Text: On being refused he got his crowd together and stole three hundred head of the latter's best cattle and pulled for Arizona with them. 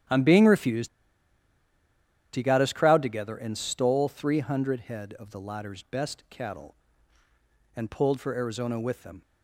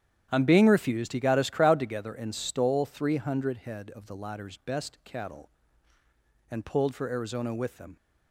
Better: second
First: starts louder than the rest; strong; until 2.5 s; 10.5 dB // pauses between "refused" and "he"; strong; at 0.8 s; 1.4 s long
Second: starts louder than the rest; strong; until 1.3 s; 10 dB

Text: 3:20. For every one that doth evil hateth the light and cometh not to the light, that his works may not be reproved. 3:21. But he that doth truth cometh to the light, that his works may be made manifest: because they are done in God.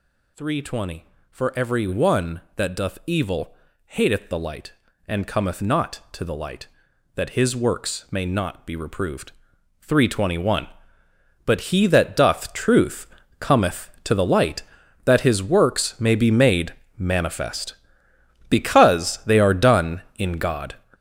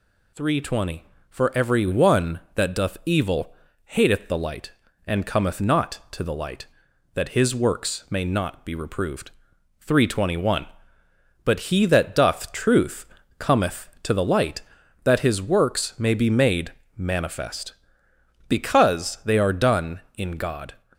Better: second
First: gets louder; strong; throughout; 8.5 dB // pauses between "evil" and "hateth"; slight; at 3.5 s; 0.32 s long // pauses between "truth" and "cometh"; slight; at 13.0 s; 0.32 s long // pauses between "made" and "manifest"; slight; at 16.7 s; 0.26 s long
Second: pauses between "evil" and "hateth"; slight; at 3.5 s; 0.32 s long // pauses between "truth" and "cometh"; slight; at 13.0 s; 0.32 s long // pauses between "made" and "manifest"; slight; at 16.7 s; 0.26 s long

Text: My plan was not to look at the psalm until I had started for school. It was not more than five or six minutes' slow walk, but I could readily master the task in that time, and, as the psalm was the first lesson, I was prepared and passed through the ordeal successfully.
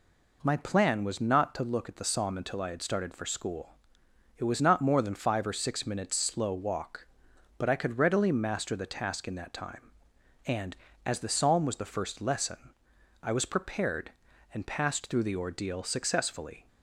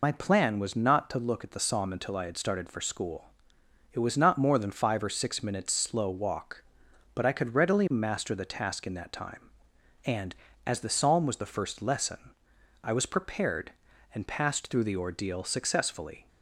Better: first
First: none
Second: loses the start of "My"; at 0.0 s; 60 ms

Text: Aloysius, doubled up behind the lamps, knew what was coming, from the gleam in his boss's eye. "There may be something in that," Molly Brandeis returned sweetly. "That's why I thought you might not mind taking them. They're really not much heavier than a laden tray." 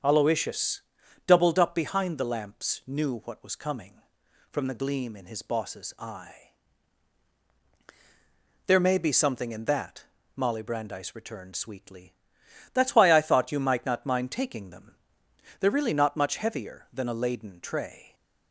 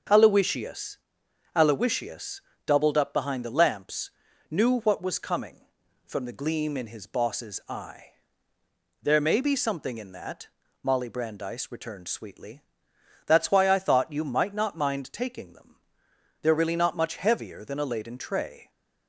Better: first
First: starts louder than the rest; strong; until 1.4 s; 7 dB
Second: starts louder than the rest; until 1.6 s; 7 dB // says "Aloysius" twice; at 1.5 s

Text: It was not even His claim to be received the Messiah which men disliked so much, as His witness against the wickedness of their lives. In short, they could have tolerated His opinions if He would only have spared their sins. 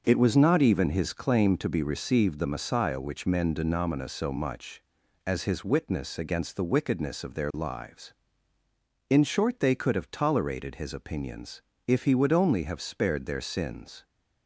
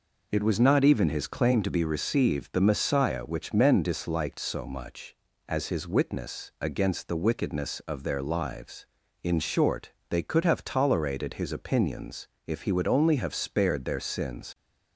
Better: second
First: starts louder than the rest; noticeable; until 1.0 s; 6 dB // says "denomina" for "disliked"; at 3.5 s // pauses between "opinions" and "if"; slight; at 11.6 s; 0.26 s long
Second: pauses between "opinions" and "if"; slight; at 12.2 s; 0.20 s long

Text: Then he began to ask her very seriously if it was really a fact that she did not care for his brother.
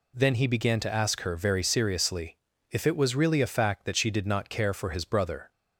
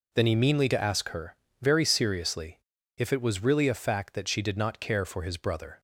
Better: first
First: pauses between "seriously" and "if"; slight; at 2.3 s; 0.34 s long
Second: says "meanly" for "began"; at 0.3 s // pauses between "her" and "very"; slight; at 1.3 s; 0.26 s long // pauses between "seriously" and "if"; at 2.5 s; 0.38 s long

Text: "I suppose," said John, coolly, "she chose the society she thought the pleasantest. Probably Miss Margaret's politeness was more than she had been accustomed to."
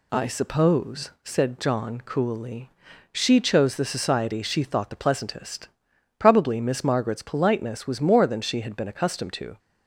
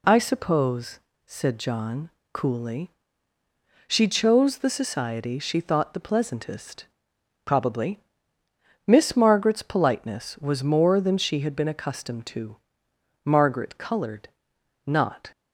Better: first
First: none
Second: pauses between "Probably" and "Miss"; noticeable; at 7.9 s; 0.86 s long // goes on to say "Margaret coloured not"; strong; from 13.2 s on; 2.0 s long

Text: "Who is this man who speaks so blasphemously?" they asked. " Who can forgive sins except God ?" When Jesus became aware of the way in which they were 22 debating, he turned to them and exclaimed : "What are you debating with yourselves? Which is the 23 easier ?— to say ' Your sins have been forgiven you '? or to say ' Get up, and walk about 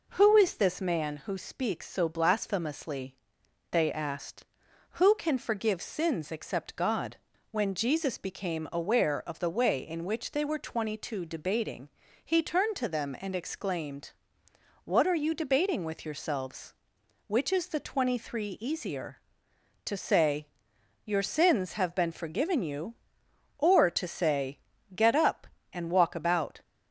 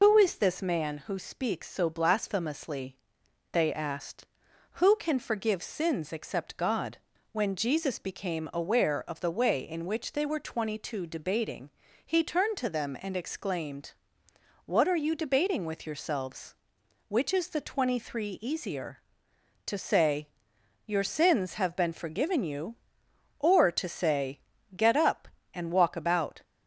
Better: first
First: none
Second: loses the start of "Who"; at 0.0 s; 110 ms

